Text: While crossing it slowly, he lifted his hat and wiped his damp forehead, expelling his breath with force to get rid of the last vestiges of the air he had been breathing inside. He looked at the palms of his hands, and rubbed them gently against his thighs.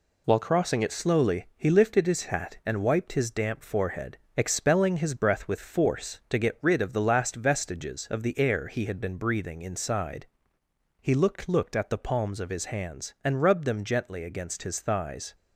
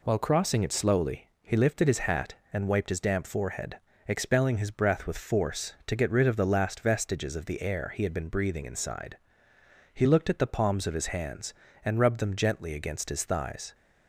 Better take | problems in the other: second | says "looked" twice; at 11.4 s

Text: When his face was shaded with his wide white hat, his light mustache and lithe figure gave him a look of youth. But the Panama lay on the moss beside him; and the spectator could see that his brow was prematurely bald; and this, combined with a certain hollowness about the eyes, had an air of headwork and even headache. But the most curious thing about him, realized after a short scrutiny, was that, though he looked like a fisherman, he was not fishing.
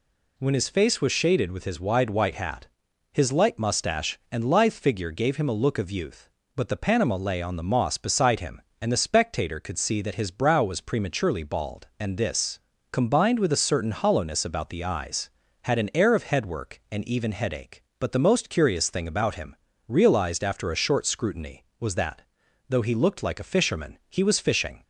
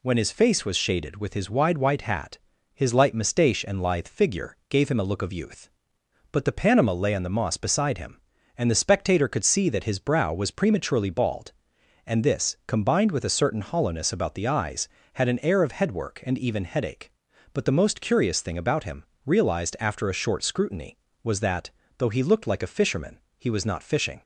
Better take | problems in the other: second | skips "not"; at 24.3 s

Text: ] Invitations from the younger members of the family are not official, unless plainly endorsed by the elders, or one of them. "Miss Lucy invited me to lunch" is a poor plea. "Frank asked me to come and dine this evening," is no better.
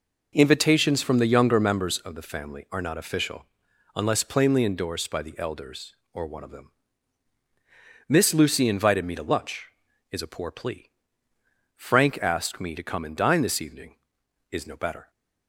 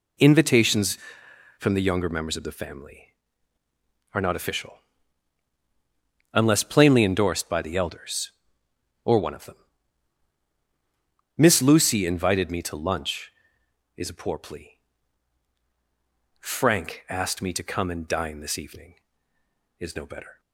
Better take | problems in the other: neither | none

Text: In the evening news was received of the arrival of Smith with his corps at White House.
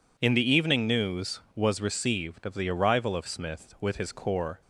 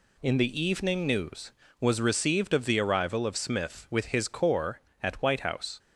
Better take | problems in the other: second | stops before "at White House"; at 4.6 s

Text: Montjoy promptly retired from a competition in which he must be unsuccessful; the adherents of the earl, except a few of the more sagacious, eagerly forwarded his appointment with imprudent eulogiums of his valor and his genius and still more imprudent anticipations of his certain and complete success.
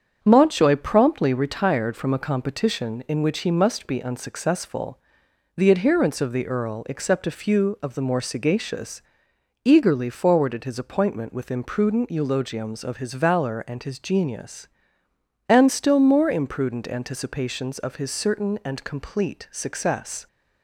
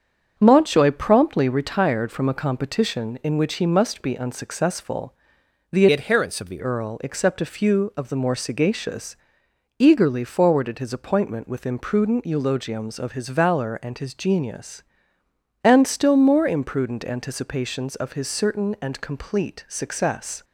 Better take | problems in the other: first | starts louder than the rest; strong; until 1.3 s; 7.5 dB; strong in the first // changes voice from "adherents" to "the"; from 5.9 to 6.6 s; 0.7 s long

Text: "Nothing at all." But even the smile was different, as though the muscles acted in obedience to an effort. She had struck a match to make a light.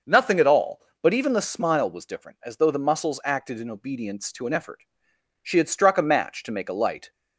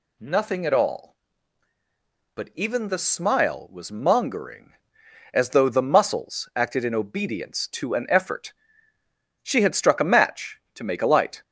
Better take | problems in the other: first | says "mongering" for "different"; at 3.9 s

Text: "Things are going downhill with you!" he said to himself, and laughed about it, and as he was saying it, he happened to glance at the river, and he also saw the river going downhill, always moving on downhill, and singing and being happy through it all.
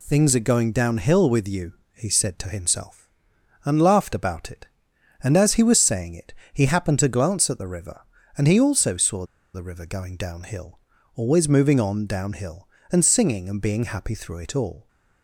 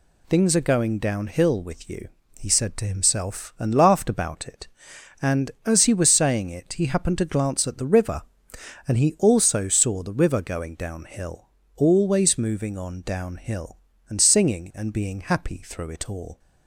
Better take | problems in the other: second | pauses between "saw" and "the"; slight; at 9.2 s; 0.28 s long

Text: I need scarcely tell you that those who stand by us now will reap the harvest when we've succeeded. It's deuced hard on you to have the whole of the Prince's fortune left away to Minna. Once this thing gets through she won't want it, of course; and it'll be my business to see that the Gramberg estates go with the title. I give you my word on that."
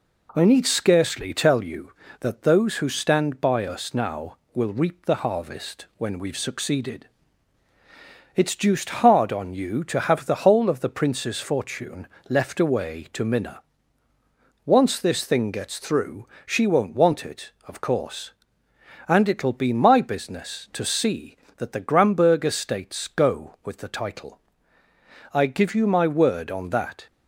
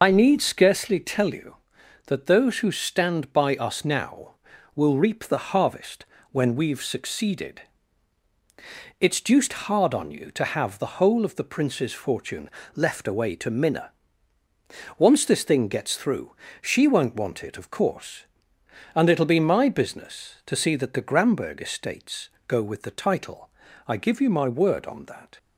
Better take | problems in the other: first | loses the start of "I"; at 0.0 s; 60 ms // pauses between "harvest" and "when"; slight; at 6.0 s; 0.28 s long // pauses between "fortune" and "left"; slight; at 12.4 s; 0.24 s long; slight in the first // pauses between "through" and "she"; slight; at 16.3 s; 0.28 s long; slight in the first // pauses between "estates" and "go"; slight; at 22.2 s; 0.18 s long

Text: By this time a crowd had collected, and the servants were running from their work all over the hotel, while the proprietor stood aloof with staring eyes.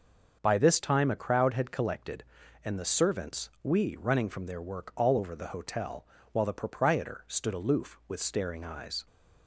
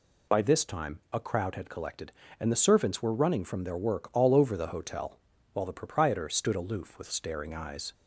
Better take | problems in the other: second | starts louder than the rest; until 1.4 s; 6.5 dB // says "we" for "were"; at 3.6 s

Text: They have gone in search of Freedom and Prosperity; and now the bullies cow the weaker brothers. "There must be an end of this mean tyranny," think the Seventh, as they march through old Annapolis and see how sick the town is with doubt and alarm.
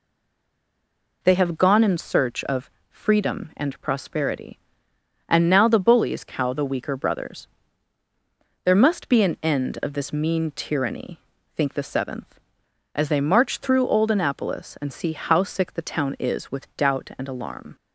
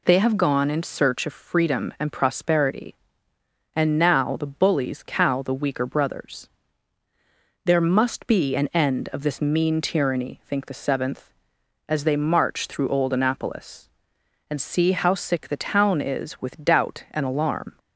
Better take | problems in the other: second | stays silent before the first word; noticeable; until 1.2 s; 1.2 s long // pauses between "of" and "Freedom"; slight; at 2.6 s; 0.20 s long

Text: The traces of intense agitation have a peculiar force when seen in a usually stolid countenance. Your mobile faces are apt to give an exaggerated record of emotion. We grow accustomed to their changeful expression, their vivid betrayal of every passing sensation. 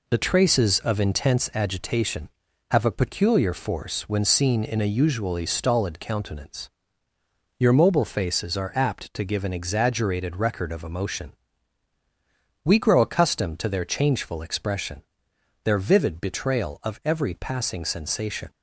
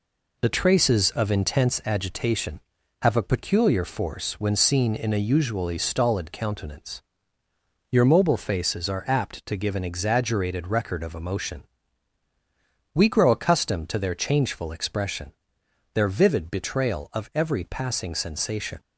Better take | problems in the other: neither | none

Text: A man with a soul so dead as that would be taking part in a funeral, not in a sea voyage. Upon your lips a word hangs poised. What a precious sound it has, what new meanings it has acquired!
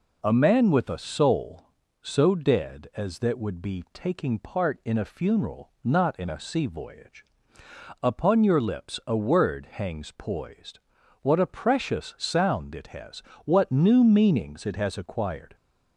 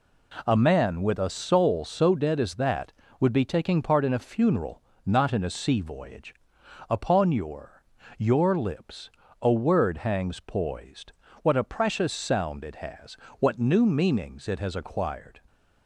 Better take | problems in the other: first | says "your" twice; at 8.1 s // pauses between "lips" and "a"; slight; at 9.1 s; 0.32 s long

